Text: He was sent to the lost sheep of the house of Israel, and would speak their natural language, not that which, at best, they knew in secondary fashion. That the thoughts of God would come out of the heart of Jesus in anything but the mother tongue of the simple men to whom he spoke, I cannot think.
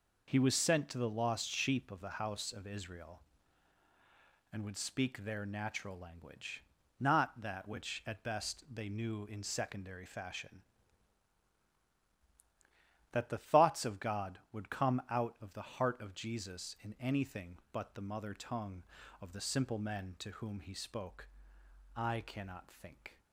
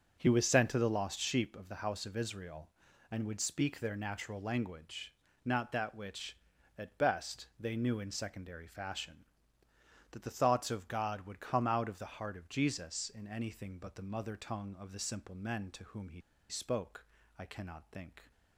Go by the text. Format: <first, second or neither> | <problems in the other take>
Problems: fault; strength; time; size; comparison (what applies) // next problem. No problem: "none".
first | starts louder than the rest; until 1.2 s; 7 dB // pauses between "he" and "spoke"; slight; at 16.1 s; 0.29 s long